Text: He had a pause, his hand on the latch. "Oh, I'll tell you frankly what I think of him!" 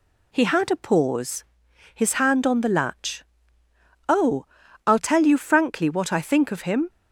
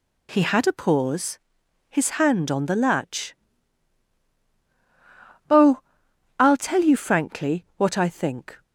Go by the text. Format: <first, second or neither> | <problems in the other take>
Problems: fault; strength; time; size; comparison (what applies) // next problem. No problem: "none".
first | stops before "of him"; at 8.6 s